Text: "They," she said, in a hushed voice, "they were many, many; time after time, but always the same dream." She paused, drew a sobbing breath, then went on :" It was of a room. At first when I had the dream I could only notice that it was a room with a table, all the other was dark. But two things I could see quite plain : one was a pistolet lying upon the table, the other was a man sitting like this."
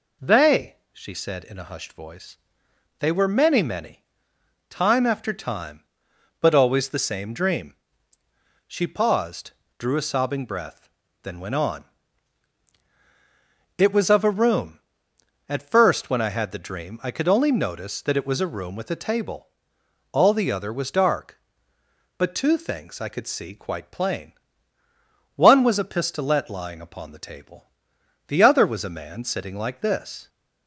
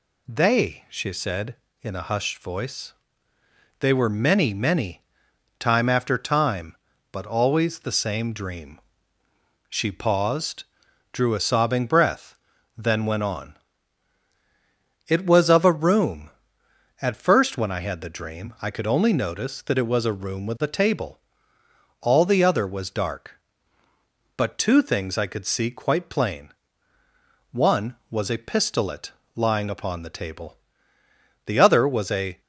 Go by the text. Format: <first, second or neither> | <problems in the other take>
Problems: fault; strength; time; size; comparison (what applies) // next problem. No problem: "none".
first | pauses between "pistolet" and "lying"; slight; at 29.1 s; 0.22 s long // stops before "man sitting like this"; at 32.3 s